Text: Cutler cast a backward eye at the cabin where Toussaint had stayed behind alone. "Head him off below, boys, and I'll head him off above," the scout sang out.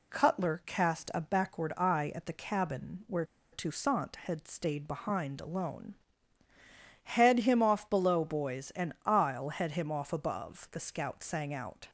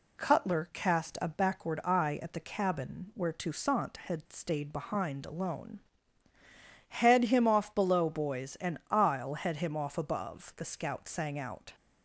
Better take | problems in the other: second | pauses between "where" and "Toussaint"; slight; at 3.2 s; 0.28 s long

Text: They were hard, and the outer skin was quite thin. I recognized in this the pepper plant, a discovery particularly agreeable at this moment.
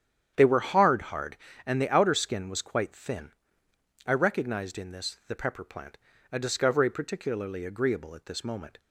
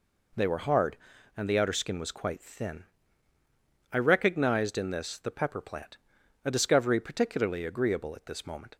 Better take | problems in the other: second | starts louder than the rest; strong; until 1.3 s; 9 dB // says "hard" twice; at 1.0 s

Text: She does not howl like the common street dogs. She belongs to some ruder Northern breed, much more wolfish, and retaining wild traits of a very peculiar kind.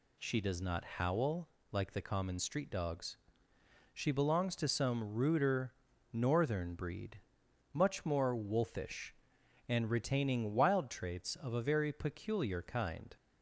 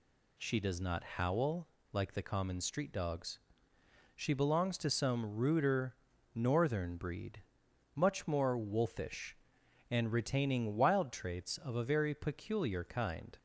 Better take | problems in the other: neither | pauses between "howl" and "like"; slight; the same in both // pauses between "ruder" and "Northern"; the same in both

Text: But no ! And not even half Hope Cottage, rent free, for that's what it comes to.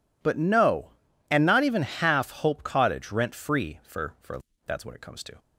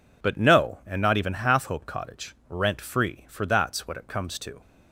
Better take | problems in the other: second | says "for" twice; at 4.2 s

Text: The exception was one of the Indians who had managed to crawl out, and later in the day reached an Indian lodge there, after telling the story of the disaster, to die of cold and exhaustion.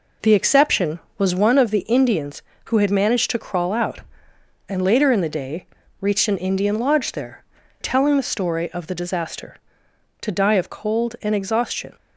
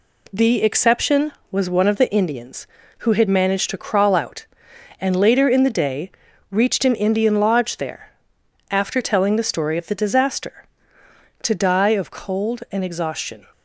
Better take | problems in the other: second | pauses between "day" and "reached"; slight; at 5.6 s; 0.34 s long; also in the second // skips "after"; at 7.6 s

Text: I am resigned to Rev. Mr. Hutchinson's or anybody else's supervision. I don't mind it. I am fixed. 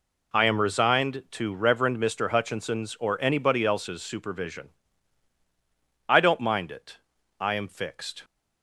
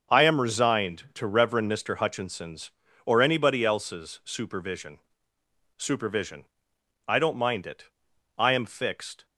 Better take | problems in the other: first | starts louder than the rest; until 1.2 s; 6.5 dB // says "supervision" twice; at 5.7 s

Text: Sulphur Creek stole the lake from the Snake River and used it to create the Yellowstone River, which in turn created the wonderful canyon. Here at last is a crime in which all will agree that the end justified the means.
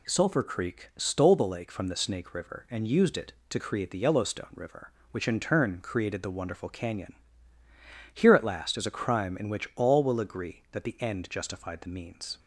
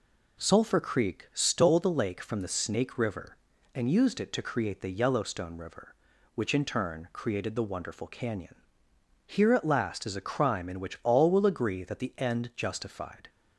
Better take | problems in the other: first | stops before "the means"; at 13.2 s

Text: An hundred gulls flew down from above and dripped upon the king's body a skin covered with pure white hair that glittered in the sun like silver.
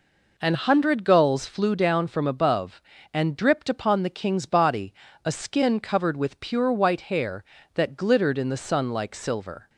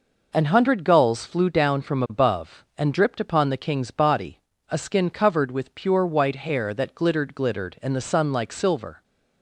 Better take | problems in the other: first | pauses between "body" and "a"; slight; at 4.3 s; 0.30 s long; slight in the first // says "glittered" twice; at 7.3 s

